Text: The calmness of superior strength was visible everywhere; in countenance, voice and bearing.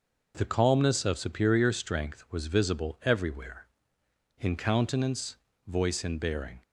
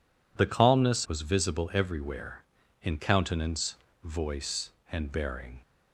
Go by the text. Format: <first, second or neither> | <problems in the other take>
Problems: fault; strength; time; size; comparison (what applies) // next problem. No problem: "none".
first | skips "of superior strength"; at 1.0 s